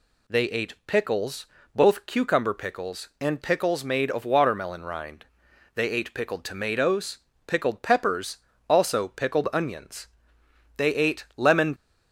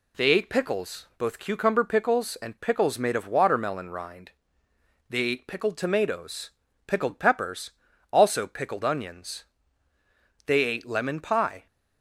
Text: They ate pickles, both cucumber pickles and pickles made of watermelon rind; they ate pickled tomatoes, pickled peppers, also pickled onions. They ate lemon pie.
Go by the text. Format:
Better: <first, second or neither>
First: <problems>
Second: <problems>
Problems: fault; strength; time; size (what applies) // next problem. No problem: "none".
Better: second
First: stops before "pie"; at 11.7 s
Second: none